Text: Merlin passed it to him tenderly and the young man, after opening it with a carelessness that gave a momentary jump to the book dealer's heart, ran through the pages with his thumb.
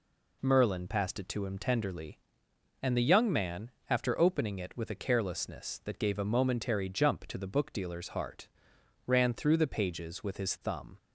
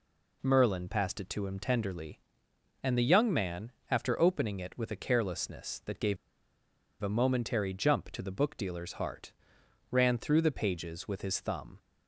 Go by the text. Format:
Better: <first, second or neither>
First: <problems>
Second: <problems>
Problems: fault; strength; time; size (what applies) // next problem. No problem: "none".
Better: first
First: none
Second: pauses between "gave" and "a"; noticeable; at 6.1 s; 0.86 s long